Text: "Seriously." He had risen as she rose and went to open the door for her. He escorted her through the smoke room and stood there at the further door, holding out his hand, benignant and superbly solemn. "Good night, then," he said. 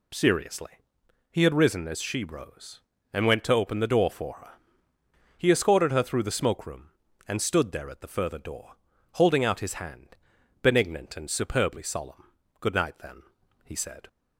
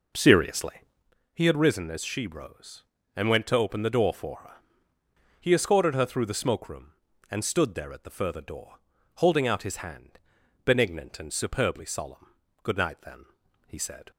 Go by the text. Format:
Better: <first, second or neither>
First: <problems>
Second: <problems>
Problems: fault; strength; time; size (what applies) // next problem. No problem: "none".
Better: first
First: none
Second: starts louder than the rest; noticeable; until 1.1 s; 5.5 dB